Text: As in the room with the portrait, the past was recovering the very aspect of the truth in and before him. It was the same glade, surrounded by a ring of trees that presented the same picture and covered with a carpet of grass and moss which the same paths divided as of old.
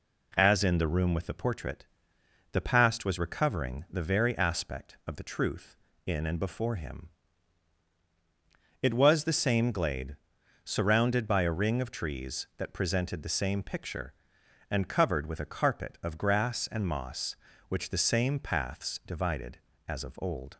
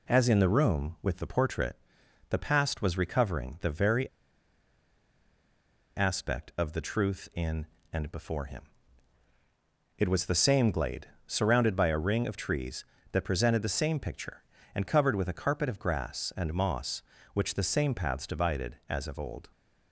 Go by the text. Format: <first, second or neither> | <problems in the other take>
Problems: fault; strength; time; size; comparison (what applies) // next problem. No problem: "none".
first | pauses between "very" and "aspect"; strong; at 4.0 s; 1.8 s long